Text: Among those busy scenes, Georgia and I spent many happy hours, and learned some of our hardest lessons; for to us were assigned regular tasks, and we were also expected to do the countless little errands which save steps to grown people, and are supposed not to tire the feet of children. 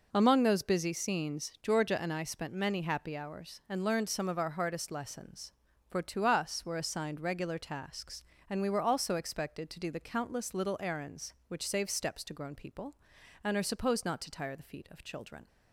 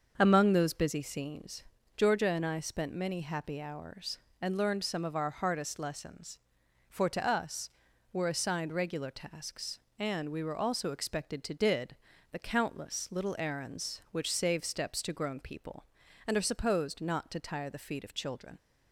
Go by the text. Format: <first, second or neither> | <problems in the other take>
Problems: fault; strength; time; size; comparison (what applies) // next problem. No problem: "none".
first | starts louder than the rest; until 1.1 s; 6.5 dB // says "did" for "do"; at 11.5 s